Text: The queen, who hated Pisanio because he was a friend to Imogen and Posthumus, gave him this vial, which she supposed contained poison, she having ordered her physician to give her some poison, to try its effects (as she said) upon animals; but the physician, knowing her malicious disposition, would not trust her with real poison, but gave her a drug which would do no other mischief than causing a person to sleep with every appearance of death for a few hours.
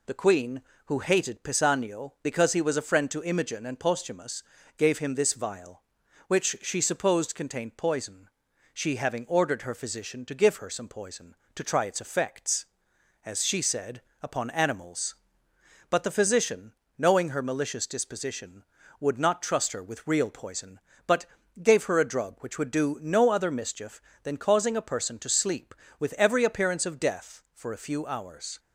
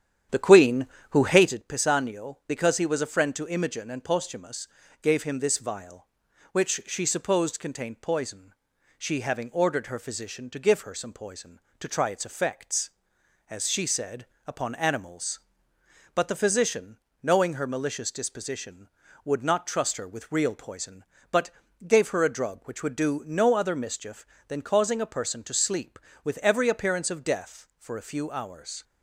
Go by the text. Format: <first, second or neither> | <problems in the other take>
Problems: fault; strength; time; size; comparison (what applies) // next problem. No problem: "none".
first | starts louder than the rest; strong; until 1.6 s; 9.5 dB // pauses between "but" and "gave"; at 21.4 s; 0.38 s long; also in the first